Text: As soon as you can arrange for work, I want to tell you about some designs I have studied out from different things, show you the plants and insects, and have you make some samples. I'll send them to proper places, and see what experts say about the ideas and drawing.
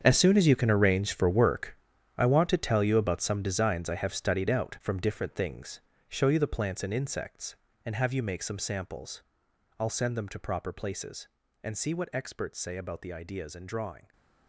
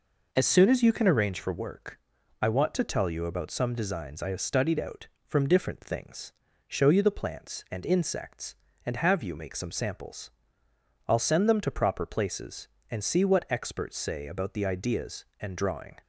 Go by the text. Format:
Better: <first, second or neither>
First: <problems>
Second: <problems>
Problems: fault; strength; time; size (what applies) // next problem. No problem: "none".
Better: second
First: gets quieter; strong; throughout; 14.5 dB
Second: none